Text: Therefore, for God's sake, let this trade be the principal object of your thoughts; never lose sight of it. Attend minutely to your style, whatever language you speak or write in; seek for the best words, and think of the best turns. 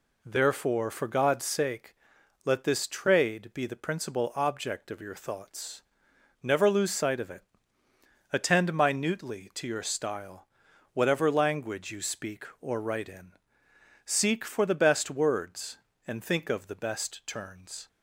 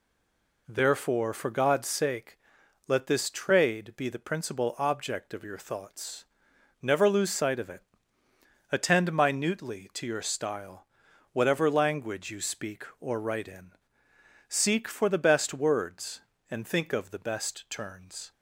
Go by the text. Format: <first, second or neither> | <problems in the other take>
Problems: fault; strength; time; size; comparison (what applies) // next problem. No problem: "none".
first | stays silent before the first word; slight; until 0.6 s; 0.6 s long